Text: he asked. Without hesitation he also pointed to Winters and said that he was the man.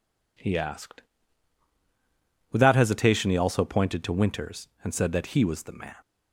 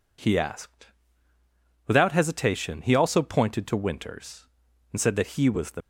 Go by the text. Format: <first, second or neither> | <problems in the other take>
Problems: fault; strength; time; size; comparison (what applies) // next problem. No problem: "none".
first | stops before "man"; at 5.8 s